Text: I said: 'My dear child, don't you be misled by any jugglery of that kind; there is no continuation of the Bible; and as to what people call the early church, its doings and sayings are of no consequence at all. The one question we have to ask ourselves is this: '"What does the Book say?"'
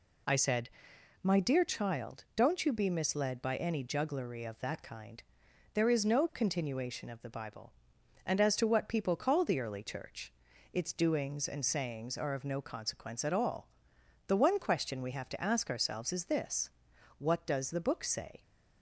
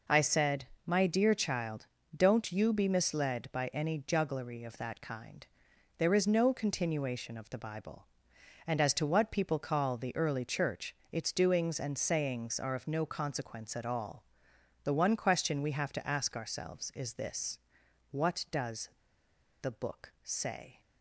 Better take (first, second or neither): first